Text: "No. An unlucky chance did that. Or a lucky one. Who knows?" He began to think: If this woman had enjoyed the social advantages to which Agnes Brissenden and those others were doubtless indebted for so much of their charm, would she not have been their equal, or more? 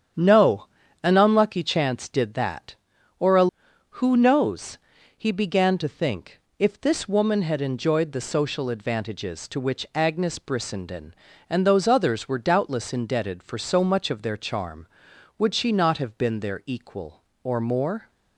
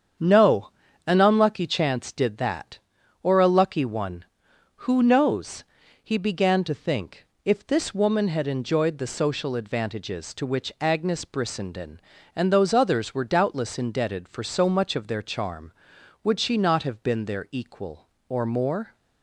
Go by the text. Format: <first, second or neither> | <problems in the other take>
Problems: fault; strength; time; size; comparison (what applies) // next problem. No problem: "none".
second | starts louder than the rest; strong; until 1.5 s; 8.5 dB; strong in the second // skips "lucky one"; at 3.7 s